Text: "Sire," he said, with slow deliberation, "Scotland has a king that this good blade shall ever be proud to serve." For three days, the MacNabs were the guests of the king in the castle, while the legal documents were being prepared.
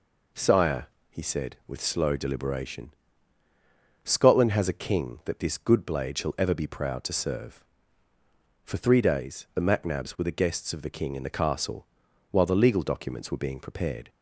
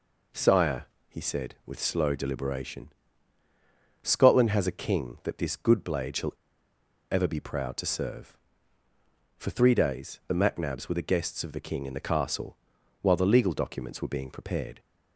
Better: first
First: none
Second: pauses between "shall" and "ever"; noticeable; at 6.3 s; 0.78 s long

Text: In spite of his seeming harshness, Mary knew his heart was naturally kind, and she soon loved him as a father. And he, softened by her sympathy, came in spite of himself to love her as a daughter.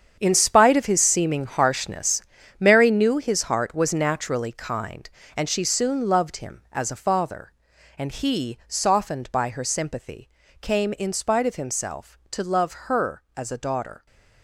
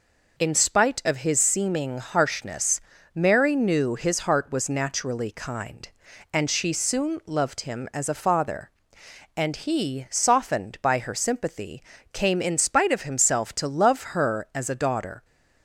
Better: second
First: gets quieter; strong; throughout; 12.5 dB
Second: none

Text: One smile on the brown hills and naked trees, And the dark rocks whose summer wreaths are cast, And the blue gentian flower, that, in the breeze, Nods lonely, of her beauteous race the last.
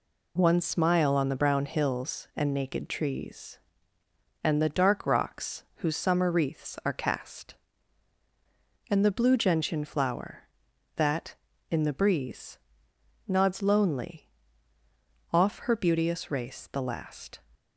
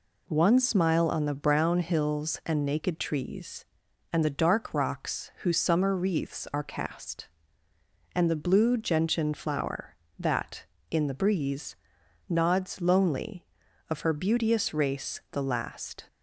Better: second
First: says "off" for "of"; at 15.3 s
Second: none

